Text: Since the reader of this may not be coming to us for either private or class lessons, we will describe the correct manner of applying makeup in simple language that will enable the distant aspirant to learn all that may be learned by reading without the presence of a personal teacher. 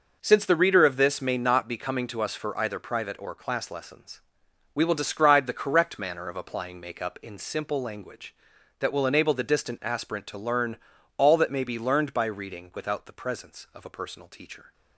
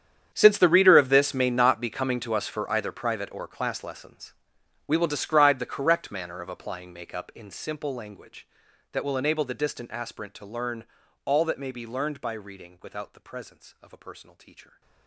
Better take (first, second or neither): first